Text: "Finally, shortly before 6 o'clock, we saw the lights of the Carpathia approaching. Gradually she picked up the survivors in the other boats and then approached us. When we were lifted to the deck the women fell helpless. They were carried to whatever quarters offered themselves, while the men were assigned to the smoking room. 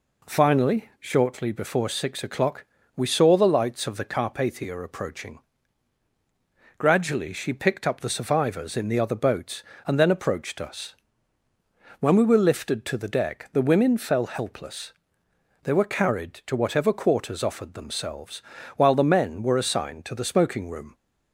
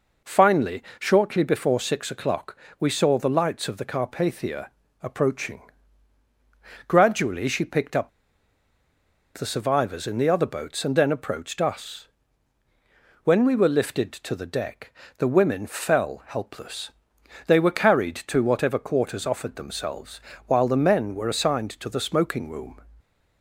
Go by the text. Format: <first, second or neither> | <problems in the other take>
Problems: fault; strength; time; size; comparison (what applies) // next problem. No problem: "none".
first | pauses between "Carpathia" and "approaching"; slight; at 4.6 s; 0.32 s long // pauses between "up" and "the"; strong; at 8.0 s; 1.2 s long // pauses between "deck" and "the"; slight; at 14.9 s; 0.26 s long